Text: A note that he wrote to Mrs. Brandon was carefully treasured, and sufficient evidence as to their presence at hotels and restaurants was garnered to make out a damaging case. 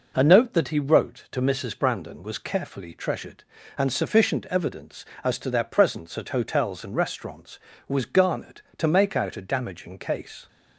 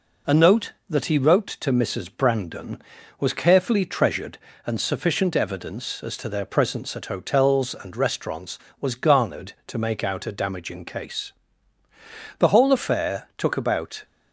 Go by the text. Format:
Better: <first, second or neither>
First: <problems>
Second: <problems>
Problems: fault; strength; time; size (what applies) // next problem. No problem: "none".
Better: first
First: none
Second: goes on to say "The whole affair took about"; from 12.3 s on; 1.6 s long